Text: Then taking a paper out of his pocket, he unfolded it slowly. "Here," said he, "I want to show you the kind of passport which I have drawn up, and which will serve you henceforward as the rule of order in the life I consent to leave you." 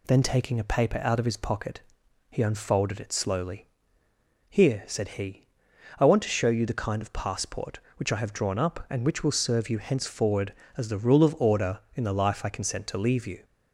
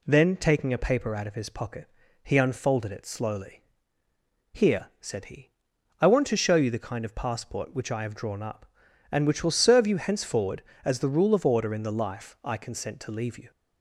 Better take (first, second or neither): neither